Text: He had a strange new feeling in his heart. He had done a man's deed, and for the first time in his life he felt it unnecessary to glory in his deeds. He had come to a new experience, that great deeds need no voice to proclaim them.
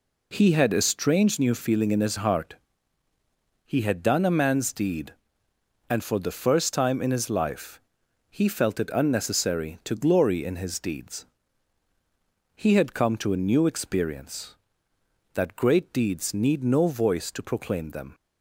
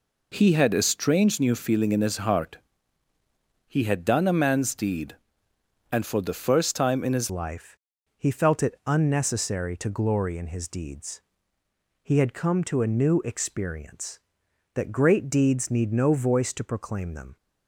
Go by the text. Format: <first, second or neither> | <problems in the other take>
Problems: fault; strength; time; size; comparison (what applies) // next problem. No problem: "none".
first | changes voice at "life"; from 7.2 s on; 10.1 s long // pauses between "life" and "he"; at 7.7 s; 0.40 s long; noticeable in the first